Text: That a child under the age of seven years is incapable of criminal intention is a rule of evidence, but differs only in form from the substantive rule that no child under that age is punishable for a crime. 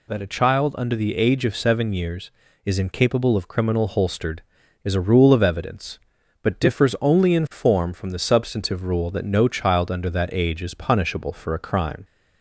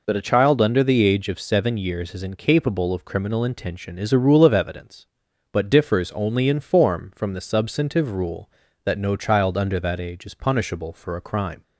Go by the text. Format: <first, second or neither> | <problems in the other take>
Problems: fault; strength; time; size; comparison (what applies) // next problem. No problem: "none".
second | says "holstered" for "intention"; at 3.8 s